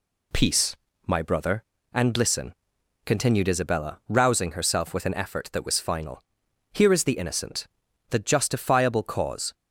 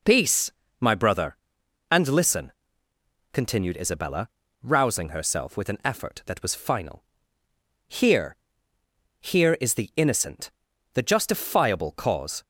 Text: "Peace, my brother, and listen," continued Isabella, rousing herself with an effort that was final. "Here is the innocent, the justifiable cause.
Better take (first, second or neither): first